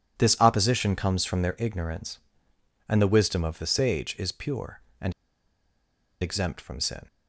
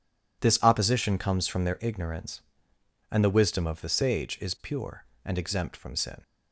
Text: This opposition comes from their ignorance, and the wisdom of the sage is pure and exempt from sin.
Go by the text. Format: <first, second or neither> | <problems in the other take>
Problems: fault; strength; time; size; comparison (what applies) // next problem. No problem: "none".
second | pauses between "and" and "exempt"; at 5.1 s; 1.0 s long